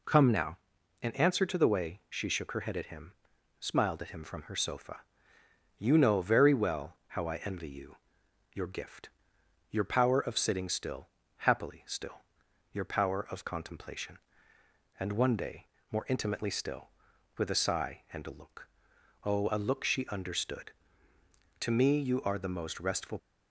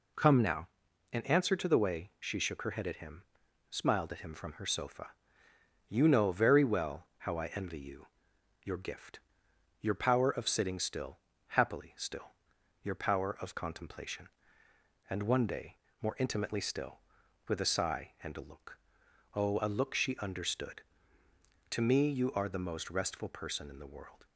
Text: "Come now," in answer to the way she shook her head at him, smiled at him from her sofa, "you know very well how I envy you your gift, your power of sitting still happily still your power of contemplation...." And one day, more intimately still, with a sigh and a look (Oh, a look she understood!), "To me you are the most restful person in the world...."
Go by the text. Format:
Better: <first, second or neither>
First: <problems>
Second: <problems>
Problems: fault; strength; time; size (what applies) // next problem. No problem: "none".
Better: second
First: pauses between "you" and "your"; noticeable; at 7.9 s; 0.56 s long // pauses between "still" and "happily"; slight; at 11.0 s; 0.28 s long // pauses between "still" and "your"; noticeable; at 12.2 s; 0.48 s long // stops before "person in the world"; at 23.1 s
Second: pauses between "you" and "your"; noticeable; at 8.0 s; 0.56 s long // pauses between "still" and "happily"; slight; at 11.1 s; 0.28 s long // pauses between "still" and "your"; noticeable; at 12.3 s; 0.48 s long